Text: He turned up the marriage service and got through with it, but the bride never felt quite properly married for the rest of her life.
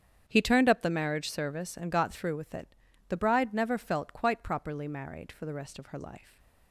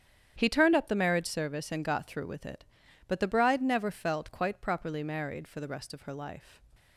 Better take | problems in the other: second | starts louder than the rest; strong; until 1.2 s; 8.5 dB; strong in the second // skips "but"; at 2.8 s // stays silent after the last word; slight; from 6.1 s on; 0.6 s long

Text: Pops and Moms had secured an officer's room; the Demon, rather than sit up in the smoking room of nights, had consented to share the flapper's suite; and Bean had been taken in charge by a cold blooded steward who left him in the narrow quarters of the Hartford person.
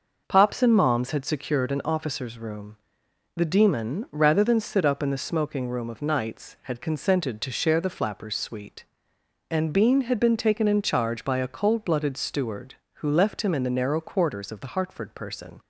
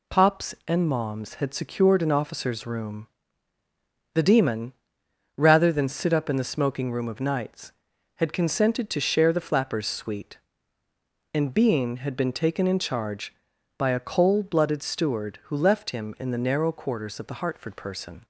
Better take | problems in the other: neither | none

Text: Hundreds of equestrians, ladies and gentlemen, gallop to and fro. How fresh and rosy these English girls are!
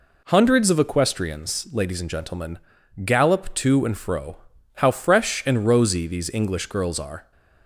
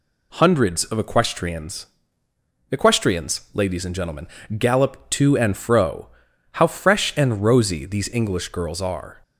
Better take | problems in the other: first | says "equestrians" twice; at 2.6 s

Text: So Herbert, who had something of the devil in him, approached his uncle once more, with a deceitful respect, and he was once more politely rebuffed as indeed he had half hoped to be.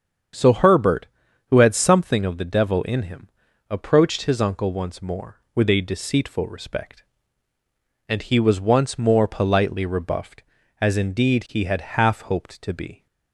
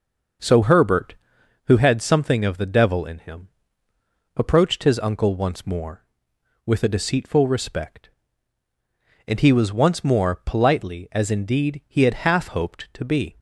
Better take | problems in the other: first | starts louder than the rest; noticeable; until 1.9 s; 6 dB; strong in the first // skips "rebuffed"; at 11.0 s

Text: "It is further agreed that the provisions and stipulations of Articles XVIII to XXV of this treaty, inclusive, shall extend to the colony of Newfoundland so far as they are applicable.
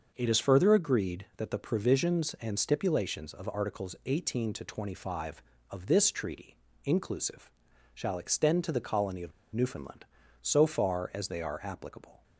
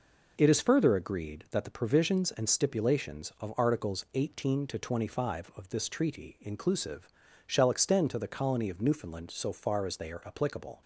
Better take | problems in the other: second | starts louder than the rest; noticeable; until 1.1 s; 6 dB // pauses between "of" and "Newfoundland"; slight; at 9.3 s; 0.21 s long

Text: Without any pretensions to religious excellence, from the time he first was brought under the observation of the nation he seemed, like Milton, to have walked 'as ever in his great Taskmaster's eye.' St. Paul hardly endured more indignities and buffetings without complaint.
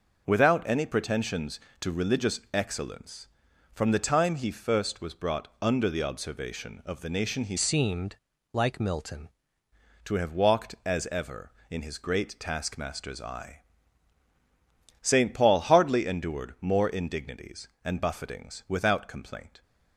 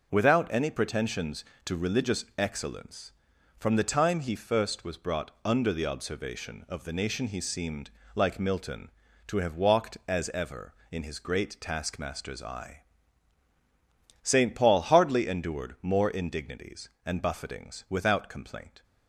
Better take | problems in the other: second | changes voice from "seemed" to "Milton"; from 7.5 to 9.2 s; 1.7 s long

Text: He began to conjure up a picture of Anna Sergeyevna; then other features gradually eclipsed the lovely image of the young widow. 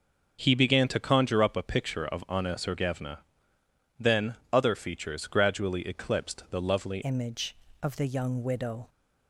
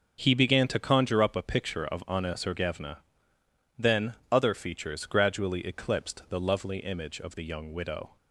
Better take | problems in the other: second | starts louder than the rest; noticeable; until 1.4 s; 6 dB; also in the second // pauses between "then" and "other"; slight; at 4.3 s; 0.18 s long; slight in the second // changes voice at "image"; from 7.0 s on; 1.8 s long

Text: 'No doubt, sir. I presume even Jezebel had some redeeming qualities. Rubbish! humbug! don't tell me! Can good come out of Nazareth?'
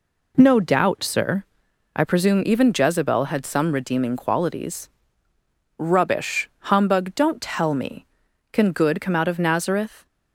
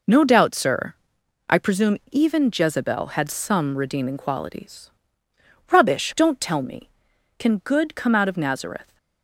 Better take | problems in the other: first | skips "humbug"; at 6.1 s

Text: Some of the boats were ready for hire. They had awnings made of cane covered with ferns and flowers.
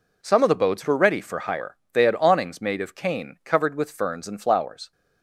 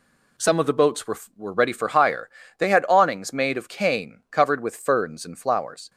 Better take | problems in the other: first | says "were" twice; at 1.3 s

